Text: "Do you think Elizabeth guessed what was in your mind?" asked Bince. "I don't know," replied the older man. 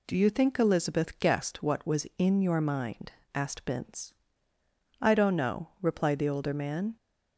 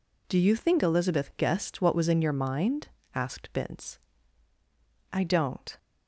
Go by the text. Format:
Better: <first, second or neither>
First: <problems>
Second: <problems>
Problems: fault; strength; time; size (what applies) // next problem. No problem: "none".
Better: first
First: none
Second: stops before "know replied the older man"; at 5.7 s